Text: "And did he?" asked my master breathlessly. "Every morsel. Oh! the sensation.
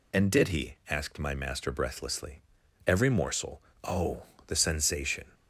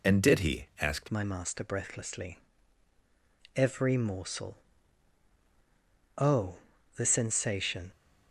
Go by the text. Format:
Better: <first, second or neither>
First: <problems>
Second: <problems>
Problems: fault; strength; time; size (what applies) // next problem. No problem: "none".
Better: first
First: none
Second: changes voice at "my"; from 1.1 s on; 6.8 s long